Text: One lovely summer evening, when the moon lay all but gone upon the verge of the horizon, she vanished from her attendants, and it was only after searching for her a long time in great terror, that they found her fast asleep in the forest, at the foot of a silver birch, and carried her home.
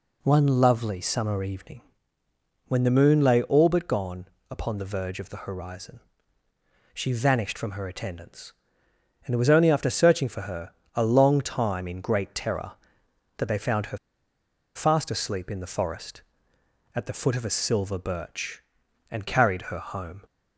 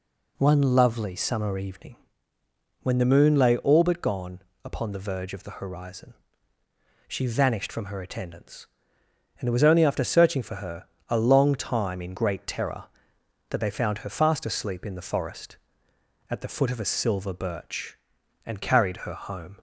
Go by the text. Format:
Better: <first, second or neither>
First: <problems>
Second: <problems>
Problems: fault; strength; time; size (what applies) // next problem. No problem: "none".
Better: second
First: pauses between "gone" and "upon"; slight; at 4.2 s; 0.24 s long // pauses between "her" and "a"; slight; at 10.7 s; 0.22 s long // pauses between "her" and "fast"; noticeable; at 13.9 s; 0.78 s long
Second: pauses between "gone" and "upon"; slight; at 4.4 s; 0.24 s long // pauses between "her" and "a"; slight; at 10.8 s; 0.22 s long